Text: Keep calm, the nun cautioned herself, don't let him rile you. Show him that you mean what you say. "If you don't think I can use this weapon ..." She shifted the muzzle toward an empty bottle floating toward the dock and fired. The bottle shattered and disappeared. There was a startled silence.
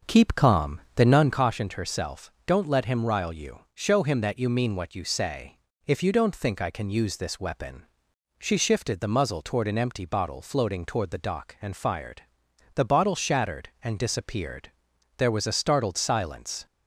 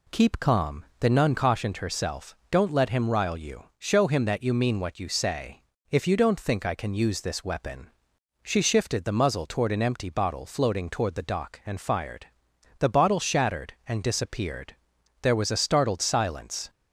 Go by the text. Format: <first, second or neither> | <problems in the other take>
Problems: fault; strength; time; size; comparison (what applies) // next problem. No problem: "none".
second | starts louder than the rest; until 1.4 s; 7 dB